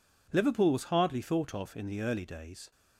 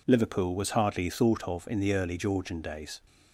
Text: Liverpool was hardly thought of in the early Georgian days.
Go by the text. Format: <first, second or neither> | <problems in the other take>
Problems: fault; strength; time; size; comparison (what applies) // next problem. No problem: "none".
second | skips "Georgian"; at 2.2 s